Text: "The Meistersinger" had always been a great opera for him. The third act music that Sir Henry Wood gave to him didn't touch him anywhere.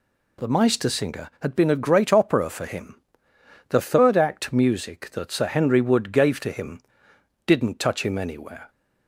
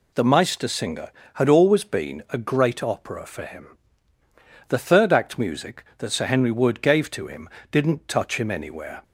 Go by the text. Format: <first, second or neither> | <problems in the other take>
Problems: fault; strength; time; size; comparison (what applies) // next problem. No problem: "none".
second | skips "always"; at 1.5 s // pauses between "him" and "didn't"; noticeable; at 6.7 s; 0.66 s long; slight in the second